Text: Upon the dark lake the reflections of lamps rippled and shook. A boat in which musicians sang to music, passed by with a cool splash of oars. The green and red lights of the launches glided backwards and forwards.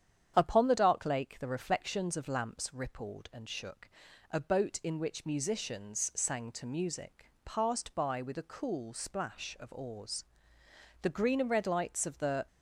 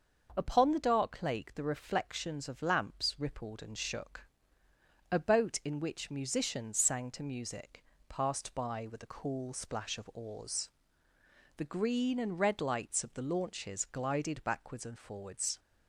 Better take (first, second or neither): second